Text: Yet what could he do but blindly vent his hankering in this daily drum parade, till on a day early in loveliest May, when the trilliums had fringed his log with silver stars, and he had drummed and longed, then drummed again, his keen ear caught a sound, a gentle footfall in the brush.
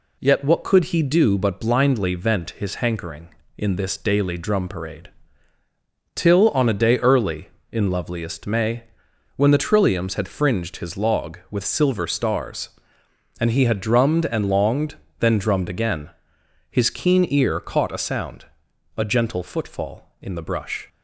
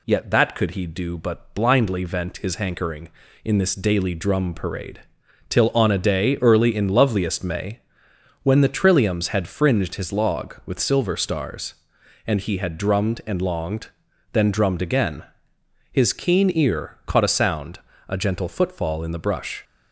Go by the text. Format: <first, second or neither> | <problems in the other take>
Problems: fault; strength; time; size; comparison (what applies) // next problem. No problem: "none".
first | says "that" for "what"; at 0.3 s